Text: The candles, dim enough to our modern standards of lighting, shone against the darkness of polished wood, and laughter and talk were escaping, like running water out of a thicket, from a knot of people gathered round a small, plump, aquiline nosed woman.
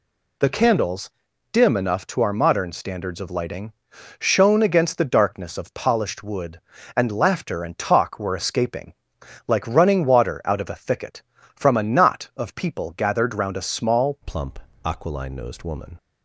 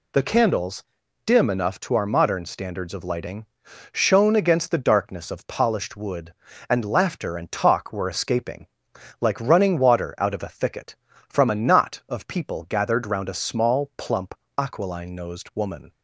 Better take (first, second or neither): second